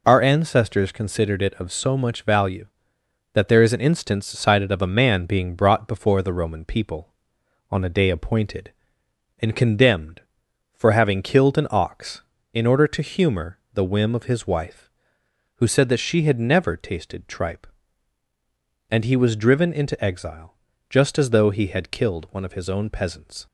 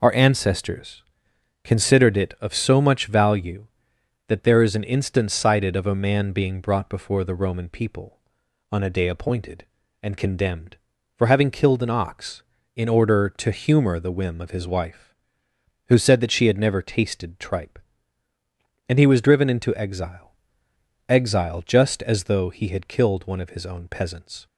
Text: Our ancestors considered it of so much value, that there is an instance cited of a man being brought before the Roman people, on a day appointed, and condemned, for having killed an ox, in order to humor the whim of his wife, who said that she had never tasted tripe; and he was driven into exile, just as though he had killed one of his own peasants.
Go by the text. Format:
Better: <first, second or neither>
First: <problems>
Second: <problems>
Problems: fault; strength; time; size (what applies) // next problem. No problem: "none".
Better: first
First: none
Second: pauses between "ancestors" and "considered"; noticeable; at 1.0 s; 0.60 s long // says "exile" twice; at 21.1 s